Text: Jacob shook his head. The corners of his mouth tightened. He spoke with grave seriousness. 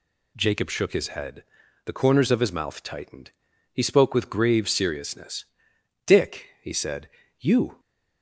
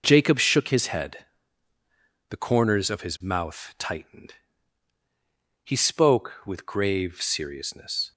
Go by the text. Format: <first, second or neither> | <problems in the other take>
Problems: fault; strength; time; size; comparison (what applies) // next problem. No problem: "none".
second | goes on to say "Dick he said you"; strong; from 6.0 s on; 1.7 s long